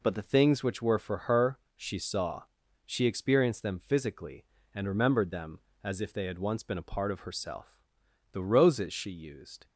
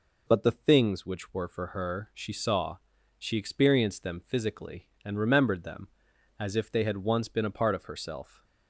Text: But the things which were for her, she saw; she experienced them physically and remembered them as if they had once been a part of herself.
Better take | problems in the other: second | goes on to say "The roses she used"; from 8.3 s on; 1.3 s long

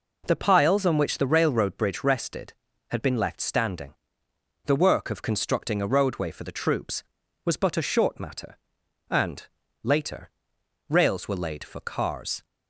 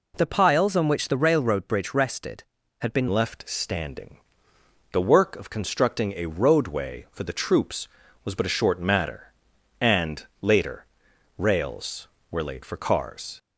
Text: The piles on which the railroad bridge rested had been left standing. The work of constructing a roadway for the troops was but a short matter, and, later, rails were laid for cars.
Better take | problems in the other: first | changes voice at "left"; from 3.0 s on; 10.3 s long

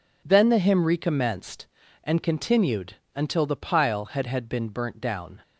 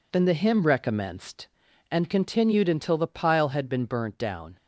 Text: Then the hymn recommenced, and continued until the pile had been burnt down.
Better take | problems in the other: second | pauses between "continued" and "until"; slight; at 2.9 s; 0.20 s long // says "had" twice; at 4.2 s

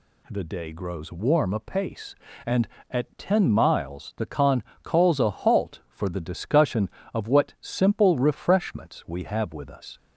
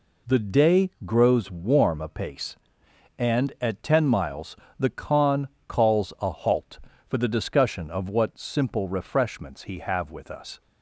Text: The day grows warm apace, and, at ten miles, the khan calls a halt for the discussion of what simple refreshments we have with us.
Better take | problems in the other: first | pauses between "day" and "grows"; slight; at 0.8 s; 0.16 s long // pauses between "khan" and "calls"; slight; at 5.4 s; 0.18 s long; slight in the first // says "he" for "we"; at 9.6 s

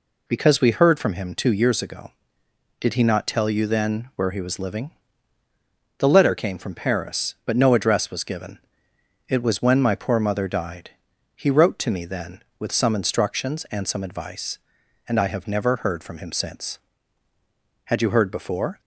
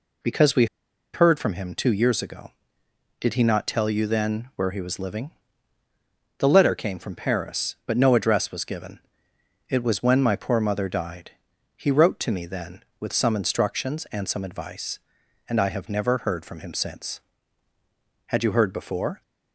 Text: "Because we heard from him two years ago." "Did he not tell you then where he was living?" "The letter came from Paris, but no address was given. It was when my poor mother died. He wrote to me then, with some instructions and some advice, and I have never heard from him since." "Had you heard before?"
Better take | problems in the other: first | pauses between "we" and "heard"; noticeable; at 0.6 s; 0.47 s long

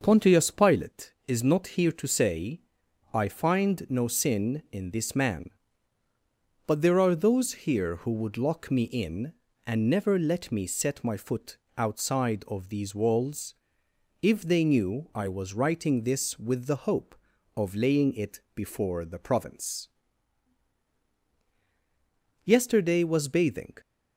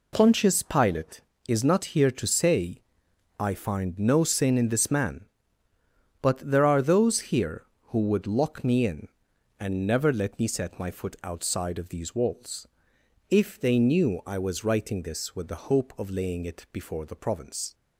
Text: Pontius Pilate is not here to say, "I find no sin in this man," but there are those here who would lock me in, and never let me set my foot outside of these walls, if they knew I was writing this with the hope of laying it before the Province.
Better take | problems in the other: second | pauses between "foot" and "outside"; slight; at 11.5 s; 0.22 s long // pauses between "it" and "before"; slight; at 18.3 s; 0.16 s long // goes on to say "Yesterday was bathing"; from 22.4 s on; 1.3 s long

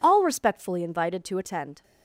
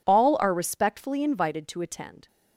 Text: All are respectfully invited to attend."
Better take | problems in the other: second | skips "are"; at 0.2 s

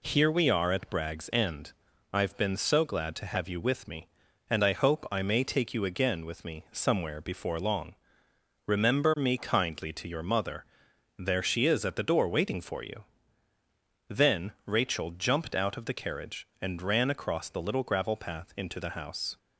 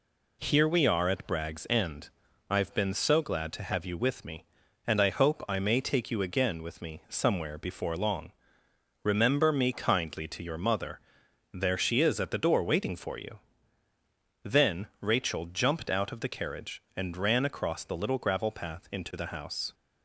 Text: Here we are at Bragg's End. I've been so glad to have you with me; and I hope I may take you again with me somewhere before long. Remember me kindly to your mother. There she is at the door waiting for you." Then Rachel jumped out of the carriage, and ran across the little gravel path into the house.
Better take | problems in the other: neither | pauses between "Then" and "Rachel"; slight; the same in both

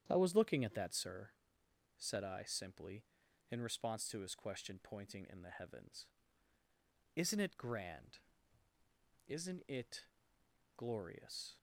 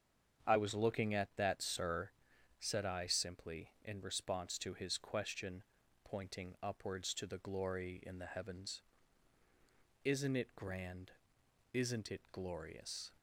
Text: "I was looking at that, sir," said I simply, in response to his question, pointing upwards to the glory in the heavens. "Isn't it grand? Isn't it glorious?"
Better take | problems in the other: second | starts louder than the rest; strong; until 1.0 s; 9 dB; strong in the second // skips "upwards to the glory"; at 5.2 s // pauses between "it" and "glorious"; noticeable; at 10.0 s; 0.72 s long

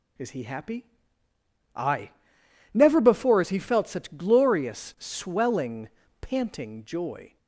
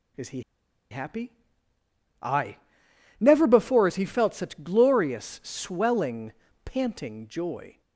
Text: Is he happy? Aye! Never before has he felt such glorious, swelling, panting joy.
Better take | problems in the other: first | pauses between "he" and "happy"; noticeable; at 0.4 s; 0.48 s long

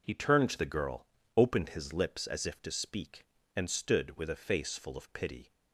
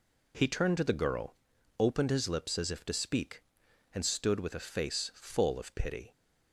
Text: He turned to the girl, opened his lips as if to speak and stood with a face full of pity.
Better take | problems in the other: neither | none

